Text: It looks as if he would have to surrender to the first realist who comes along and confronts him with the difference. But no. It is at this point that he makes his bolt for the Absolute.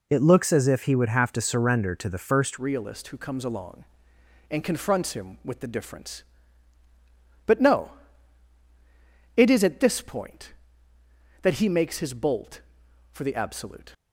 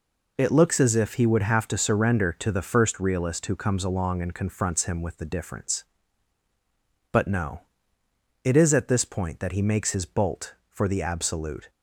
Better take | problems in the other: second | changes voice at "realist"; from 2.5 s on; 11.4 s long

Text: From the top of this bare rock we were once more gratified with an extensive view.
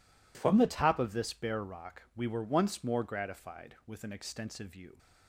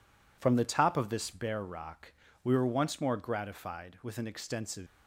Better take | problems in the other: first | pauses between "rock" and "we"; slight; at 2.1 s; 0.32 s long // stops before "view"; at 4.8 s

